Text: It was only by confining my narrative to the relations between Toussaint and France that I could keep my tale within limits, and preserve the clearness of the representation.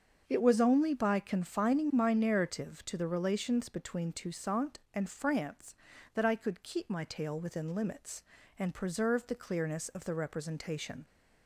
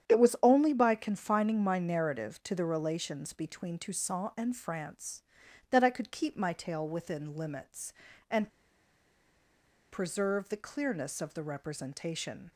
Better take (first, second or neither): first